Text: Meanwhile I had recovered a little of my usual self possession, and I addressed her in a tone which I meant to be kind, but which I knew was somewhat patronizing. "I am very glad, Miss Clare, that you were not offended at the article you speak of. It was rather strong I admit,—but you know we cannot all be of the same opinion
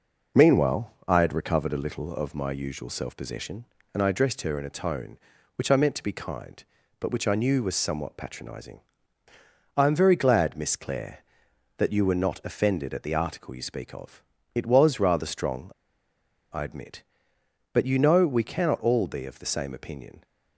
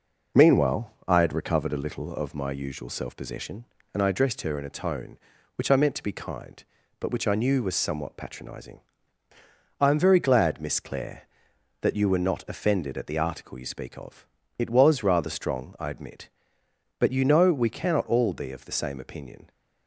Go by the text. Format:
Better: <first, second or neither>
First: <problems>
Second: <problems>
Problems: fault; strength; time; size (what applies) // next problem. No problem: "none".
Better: second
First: pauses between "Meanwhile" and "I"; slight; at 0.9 s; 0.16 s long // pauses between "strong" and "I"; noticeable; at 15.6 s; 0.83 s long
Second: pauses between "Meanwhile" and "I"; slight; at 0.9 s; 0.16 s long